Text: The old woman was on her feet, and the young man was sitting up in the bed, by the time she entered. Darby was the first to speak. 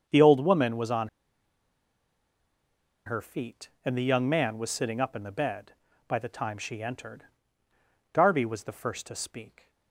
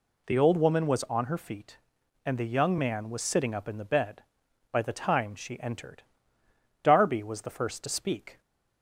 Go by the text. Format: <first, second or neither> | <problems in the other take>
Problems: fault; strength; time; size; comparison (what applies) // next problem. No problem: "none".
second | starts louder than the rest; until 1.1 s; 7 dB // pauses between "on" and "her"; strong; at 1.0 s; 1.9 s long